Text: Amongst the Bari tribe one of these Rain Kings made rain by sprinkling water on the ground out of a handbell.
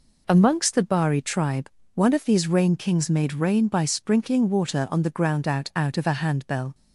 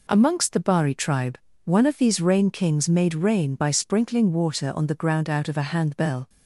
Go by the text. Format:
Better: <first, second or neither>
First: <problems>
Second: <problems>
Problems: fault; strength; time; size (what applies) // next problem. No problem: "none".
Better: second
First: pauses between "tribe" and "one"; slight; at 1.6 s; 0.24 s long // says "out" twice; at 5.7 s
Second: pauses between "tribe" and "one"; slight; at 1.3 s; 0.28 s long